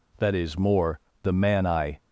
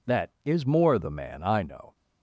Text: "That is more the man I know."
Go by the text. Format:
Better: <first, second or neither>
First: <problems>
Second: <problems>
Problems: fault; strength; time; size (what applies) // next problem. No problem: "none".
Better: second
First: pauses between "more" and "the"; slight; at 0.9 s; 0.24 s long // stops before "know"; at 1.9 s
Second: none